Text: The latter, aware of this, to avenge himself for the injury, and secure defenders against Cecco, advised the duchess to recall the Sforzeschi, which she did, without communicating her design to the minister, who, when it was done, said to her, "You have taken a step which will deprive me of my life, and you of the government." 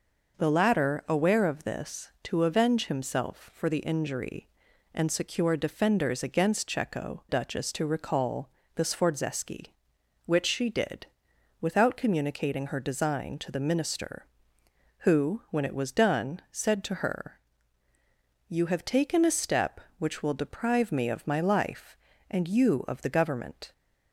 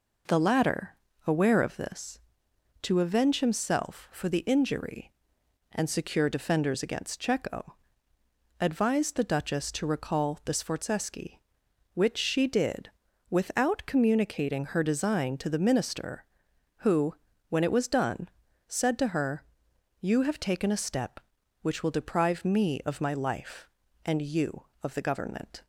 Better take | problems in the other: second | skips "advised the"; at 7.2 s // pauses between "recall" and "the"; slight; at 8.5 s; 0.24 s long

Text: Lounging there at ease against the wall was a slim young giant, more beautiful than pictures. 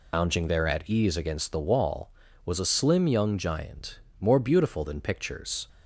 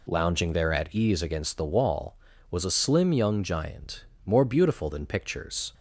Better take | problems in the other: second | loses the start of "Lounging"; at 0.1 s; 115 ms

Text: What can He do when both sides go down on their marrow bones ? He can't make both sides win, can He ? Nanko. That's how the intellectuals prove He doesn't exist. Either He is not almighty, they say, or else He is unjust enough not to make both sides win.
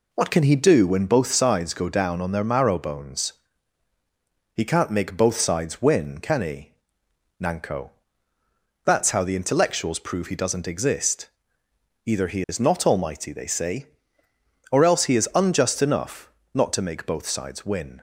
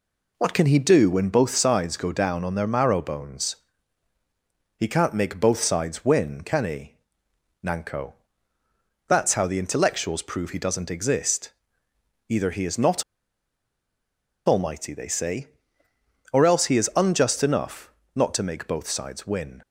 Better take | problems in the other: first | pauses between "not" and "almighty"; strong; at 13.0 s; 1.4 s long // pauses between "enough" and "not"; slight; at 17.9 s; 0.24 s long; slight in the first

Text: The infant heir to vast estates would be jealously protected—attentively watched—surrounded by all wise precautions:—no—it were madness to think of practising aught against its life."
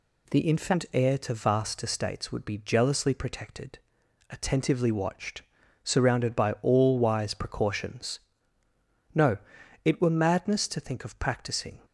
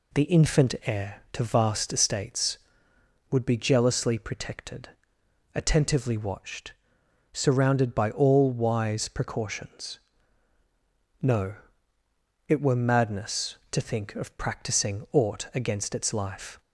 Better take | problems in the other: second | stops before "aught against its life"; at 11.8 s

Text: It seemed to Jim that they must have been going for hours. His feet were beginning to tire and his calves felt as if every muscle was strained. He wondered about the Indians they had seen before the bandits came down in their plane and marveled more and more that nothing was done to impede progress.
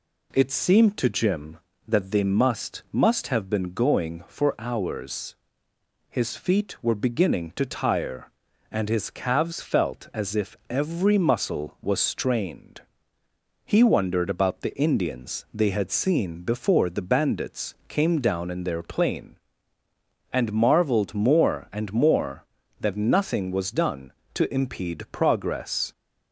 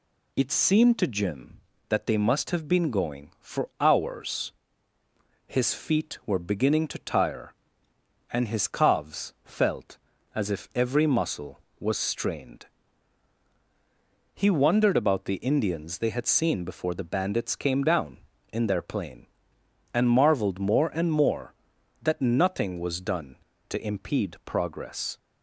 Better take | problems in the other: second | says "must" twice; at 2.8 s // pauses between "bandits" and "came"; slight; at 17.7 s; 0.16 s long

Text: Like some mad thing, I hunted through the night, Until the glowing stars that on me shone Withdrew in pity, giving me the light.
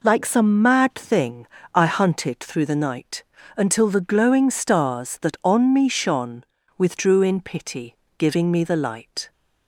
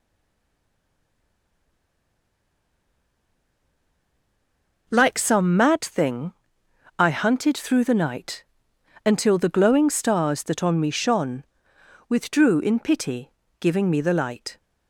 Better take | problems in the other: first | stays silent before the first word; strong; until 4.8 s; 4.8 s long // pauses between "shone" and "Withdrew"; noticeable; at 11.4 s; 0.64 s long; slight in the first

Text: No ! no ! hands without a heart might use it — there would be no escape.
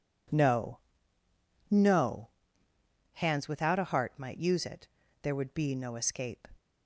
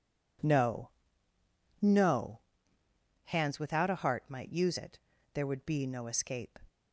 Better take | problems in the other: neither | none

